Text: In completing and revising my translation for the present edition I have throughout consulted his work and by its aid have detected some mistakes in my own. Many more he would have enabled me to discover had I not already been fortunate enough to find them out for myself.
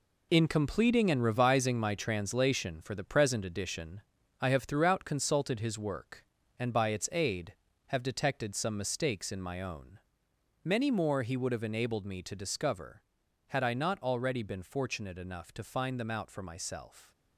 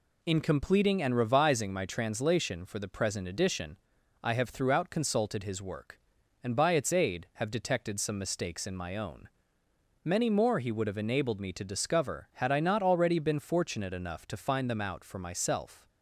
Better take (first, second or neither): second